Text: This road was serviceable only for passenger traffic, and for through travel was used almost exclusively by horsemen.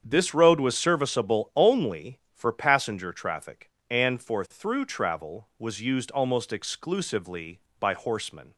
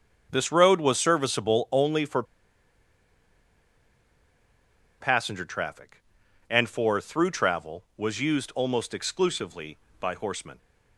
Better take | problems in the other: first | starts louder than the rest; strong; until 1.3 s; 7.5 dB; strong in the first // pauses between "for" and "passenger"; strong; at 2.2 s; 2.7 s long

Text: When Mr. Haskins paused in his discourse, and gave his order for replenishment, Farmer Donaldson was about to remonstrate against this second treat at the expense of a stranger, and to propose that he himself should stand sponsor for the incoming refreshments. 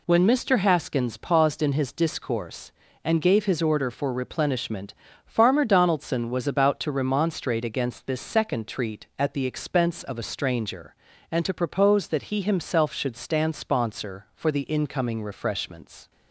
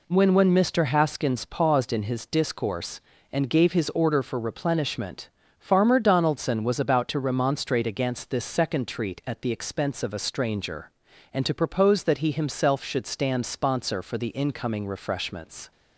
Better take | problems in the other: first | says "When" twice; at 0.3 s

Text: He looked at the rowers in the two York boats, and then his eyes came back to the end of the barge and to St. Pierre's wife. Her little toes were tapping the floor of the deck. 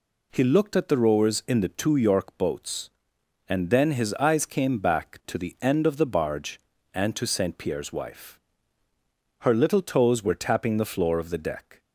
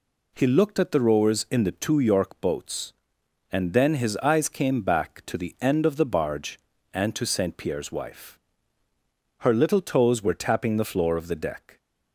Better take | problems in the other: neither | none

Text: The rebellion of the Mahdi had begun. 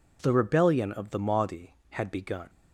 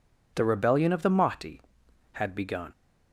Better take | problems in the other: neither | none

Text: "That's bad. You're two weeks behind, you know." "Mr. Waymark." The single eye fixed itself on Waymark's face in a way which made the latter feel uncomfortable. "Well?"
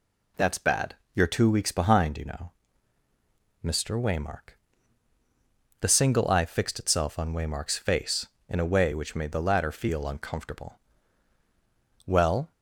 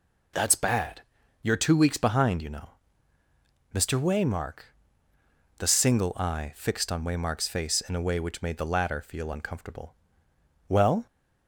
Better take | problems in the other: first | skips "itself"; at 6.9 s

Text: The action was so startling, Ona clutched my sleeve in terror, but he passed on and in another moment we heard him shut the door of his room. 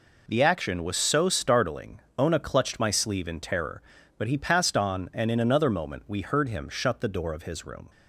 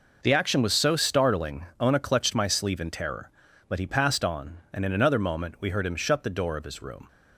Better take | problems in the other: neither | none

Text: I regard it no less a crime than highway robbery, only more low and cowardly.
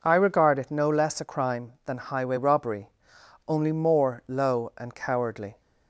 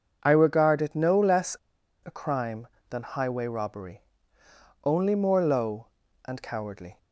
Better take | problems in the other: first | pauses between "less" and "a"; noticeable; at 1.5 s; 0.49 s long

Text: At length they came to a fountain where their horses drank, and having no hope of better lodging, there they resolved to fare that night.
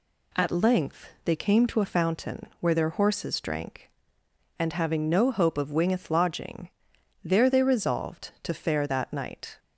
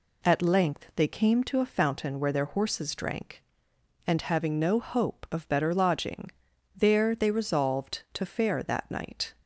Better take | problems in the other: second | says "wingeth" for "better"; at 5.7 s

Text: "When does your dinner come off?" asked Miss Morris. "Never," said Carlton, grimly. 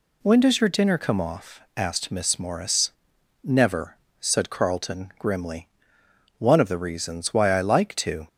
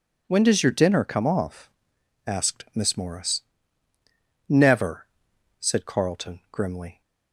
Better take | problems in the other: second | goes on to say "One of the reasons why I like to"; strong; from 6.3 s on; 1.9 s long

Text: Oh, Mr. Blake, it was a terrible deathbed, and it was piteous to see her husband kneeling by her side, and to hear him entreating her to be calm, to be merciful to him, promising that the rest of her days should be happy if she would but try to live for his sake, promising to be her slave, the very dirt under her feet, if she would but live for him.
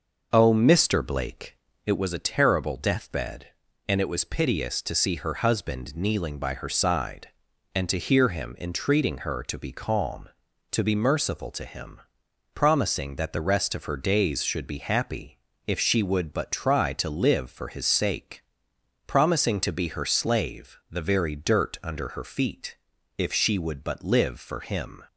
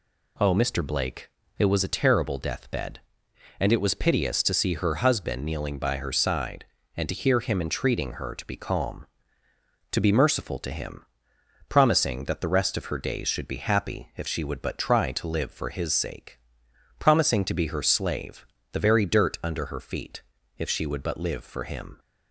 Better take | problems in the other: second | starts louder than the rest; noticeable; until 2.2 s; 6 dB // pauses between "happy" and "if"; slight; at 15.3 s; 0.26 s long

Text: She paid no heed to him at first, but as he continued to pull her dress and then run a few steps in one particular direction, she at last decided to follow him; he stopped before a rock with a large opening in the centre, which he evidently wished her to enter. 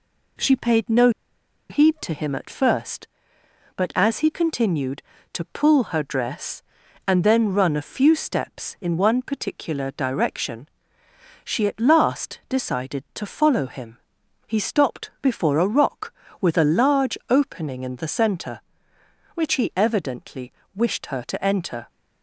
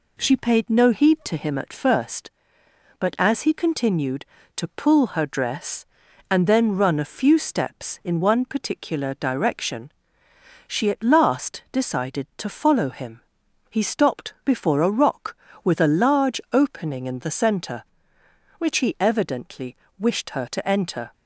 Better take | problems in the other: second | pauses between "no" and "heed"; noticeable; at 1.0 s; 0.60 s long // pauses between "evidently" and "wished"; slight; at 20.5 s; 0.24 s long; slight in the second

